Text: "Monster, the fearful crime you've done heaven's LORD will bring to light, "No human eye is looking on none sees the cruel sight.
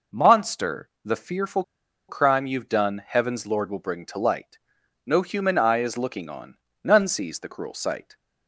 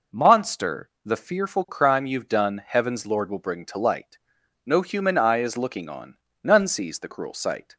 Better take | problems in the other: second | pauses between "fearful" and "crime"; noticeable; at 1.6 s; 0.46 s long // pauses between "on" and "none"; slight; at 6.5 s; 0.26 s long; slight in the second

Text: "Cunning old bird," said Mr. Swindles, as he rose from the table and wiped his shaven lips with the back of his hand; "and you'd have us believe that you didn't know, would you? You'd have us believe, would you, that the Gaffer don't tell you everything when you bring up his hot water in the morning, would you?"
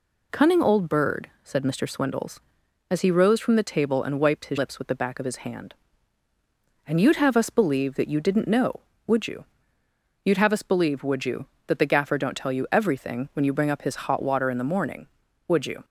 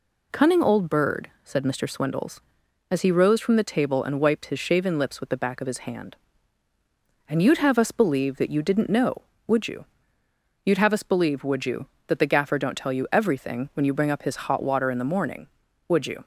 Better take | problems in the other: second | skips "shaven"; at 4.5 s

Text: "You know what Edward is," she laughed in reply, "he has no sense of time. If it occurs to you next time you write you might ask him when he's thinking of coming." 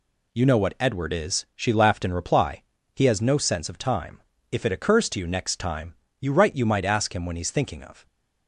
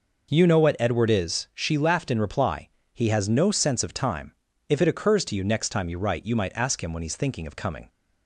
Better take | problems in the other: second | pauses between "time" and "you"; slight; at 5.9 s; 0.24 s long // stops before "coming"; at 8.0 s

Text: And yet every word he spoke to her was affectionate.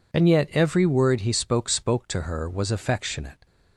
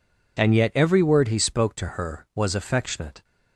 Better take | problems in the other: second | says "spoke" twice; at 1.6 s

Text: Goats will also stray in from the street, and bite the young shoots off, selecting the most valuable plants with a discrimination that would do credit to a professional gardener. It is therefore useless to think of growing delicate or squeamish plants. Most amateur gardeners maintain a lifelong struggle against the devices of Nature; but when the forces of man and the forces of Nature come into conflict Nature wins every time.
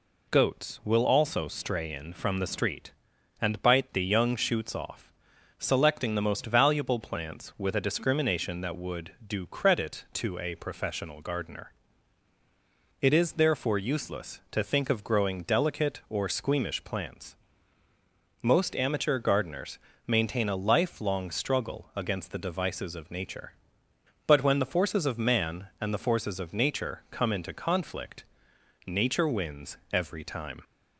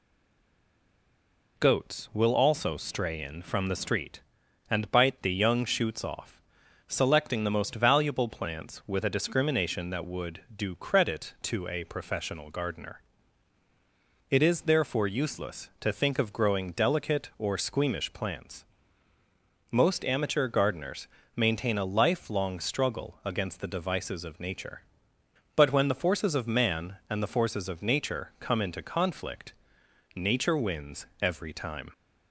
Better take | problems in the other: first | stays silent before the first word; noticeable; until 1.5 s; 1.5 s long // pauses between "gardeners" and "maintain"; slight; at 21.0 s; 0.30 s long; slight in the first // pauses between "conflict" and "Nature"; noticeable; at 29.5 s; 0.60 s long; noticeable in the first // pauses between "wins" and "every"; slight; at 31.0 s; 0.16 s long; slight in the first

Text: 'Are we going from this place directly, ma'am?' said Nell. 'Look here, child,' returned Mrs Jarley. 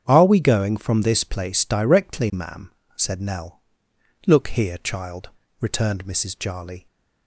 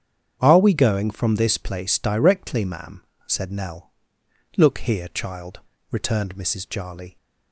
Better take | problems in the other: neither | starts louder than the rest; strong; the same in both

